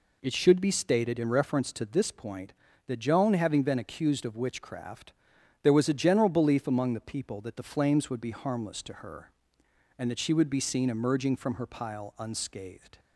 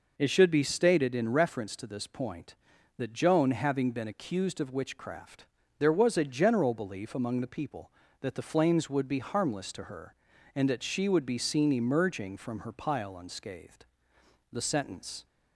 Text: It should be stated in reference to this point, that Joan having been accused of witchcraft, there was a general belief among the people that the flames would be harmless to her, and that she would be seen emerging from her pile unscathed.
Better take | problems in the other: first | goes on to say "The sentence"; noticeable; from 14.5 s on; 0.74 s long

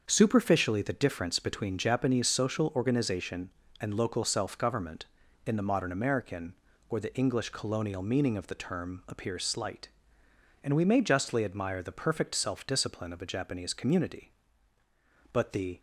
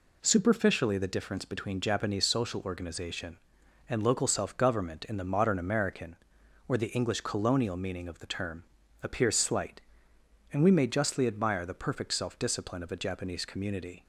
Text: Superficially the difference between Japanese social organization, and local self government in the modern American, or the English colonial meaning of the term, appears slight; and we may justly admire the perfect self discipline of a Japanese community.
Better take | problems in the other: second | starts louder than the rest; until 1.0 s; 7 dB // goes on to say "But the"; slight; from 15.3 s on; 0.48 s long

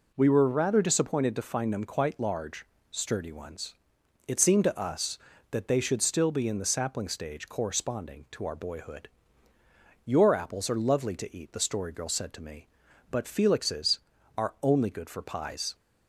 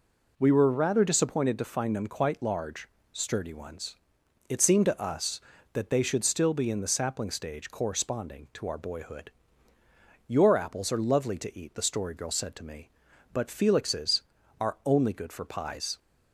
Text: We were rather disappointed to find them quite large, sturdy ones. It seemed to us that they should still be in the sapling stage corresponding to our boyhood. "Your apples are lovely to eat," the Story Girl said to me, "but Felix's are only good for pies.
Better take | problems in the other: neither | none

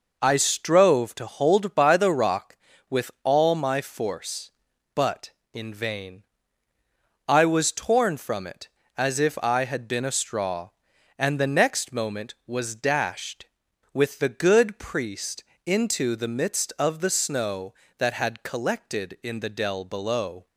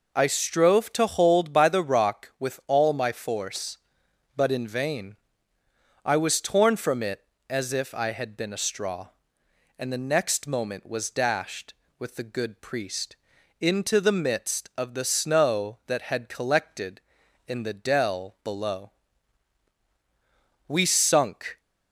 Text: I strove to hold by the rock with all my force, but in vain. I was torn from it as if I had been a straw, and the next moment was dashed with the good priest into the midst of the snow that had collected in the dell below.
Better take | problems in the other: first | pauses between "priest" and "into"; at 13.1 s; 0.42 s long; slight in the first // goes on to say "We sunk"; noticeable; from 20.6 s on; 0.92 s long

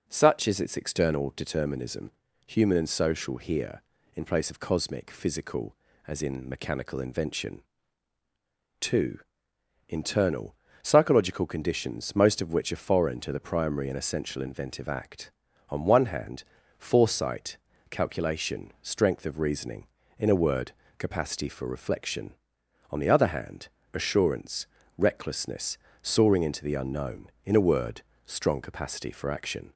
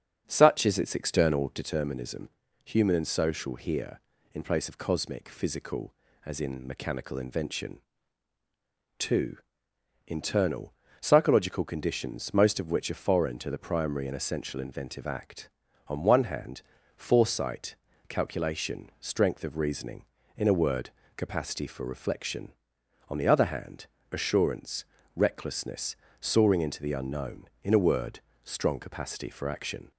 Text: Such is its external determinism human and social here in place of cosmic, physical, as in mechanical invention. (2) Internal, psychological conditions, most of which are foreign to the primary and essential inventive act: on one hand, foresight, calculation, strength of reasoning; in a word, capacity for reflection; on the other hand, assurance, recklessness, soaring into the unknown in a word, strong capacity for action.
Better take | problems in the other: first | starts louder than the rest; until 1.7 s; 7 dB // pauses between "determinism" and "human"; at 2.2 s; 0.38 s long; also in the first

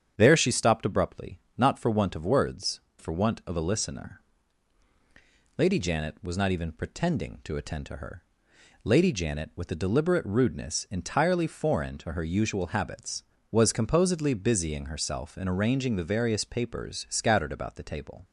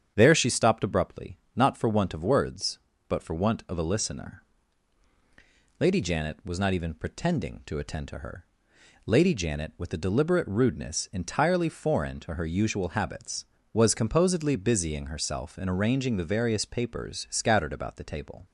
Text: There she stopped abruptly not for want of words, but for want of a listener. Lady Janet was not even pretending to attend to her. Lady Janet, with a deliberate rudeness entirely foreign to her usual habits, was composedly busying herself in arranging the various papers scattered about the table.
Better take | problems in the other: second | starts louder than the rest; strong; until 1.1 s; 8.5 dB; strong in the second // pauses between "abruptly" and "not"; slight; at 1.3 s; 0.20 s long; slight in the second // skips "but"; at 2.9 s

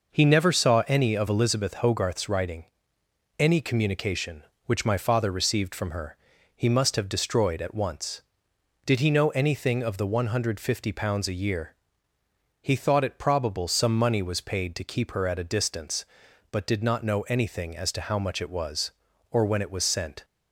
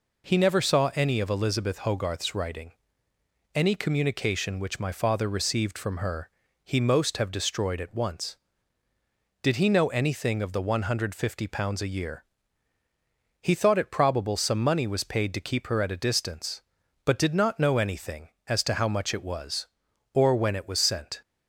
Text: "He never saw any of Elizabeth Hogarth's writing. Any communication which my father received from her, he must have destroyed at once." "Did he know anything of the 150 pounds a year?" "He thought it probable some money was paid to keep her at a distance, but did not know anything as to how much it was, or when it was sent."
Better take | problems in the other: first | says "most" for "must"; at 6.7 s

